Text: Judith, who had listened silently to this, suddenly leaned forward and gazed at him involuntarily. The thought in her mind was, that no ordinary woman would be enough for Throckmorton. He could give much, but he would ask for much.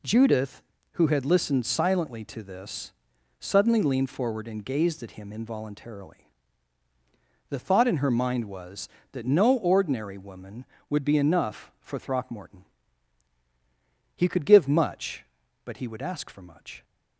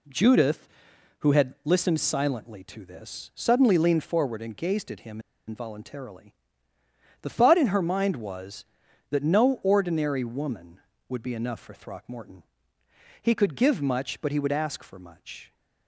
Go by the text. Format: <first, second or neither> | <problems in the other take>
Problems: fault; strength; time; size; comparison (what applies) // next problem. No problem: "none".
first | pauses between "him" and "involuntarily"; slight; at 5.1 s; 0.28 s long